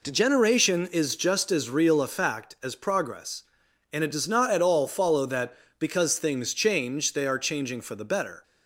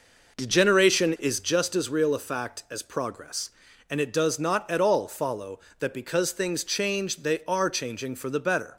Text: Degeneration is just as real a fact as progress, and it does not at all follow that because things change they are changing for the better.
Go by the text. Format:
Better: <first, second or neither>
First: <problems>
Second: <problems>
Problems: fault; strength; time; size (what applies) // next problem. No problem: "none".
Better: first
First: none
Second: starts louder than the rest; noticeable; until 1.5 s; 5.5 dB